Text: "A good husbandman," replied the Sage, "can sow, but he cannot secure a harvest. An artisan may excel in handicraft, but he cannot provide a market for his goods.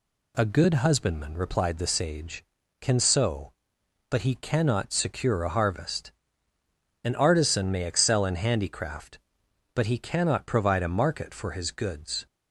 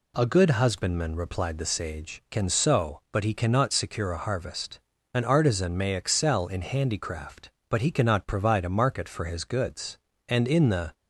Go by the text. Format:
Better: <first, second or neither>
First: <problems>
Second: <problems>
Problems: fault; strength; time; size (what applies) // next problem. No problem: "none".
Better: first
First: none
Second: goes on to say "And in the"; noticeable; from 10.2 s on; 0.64 s long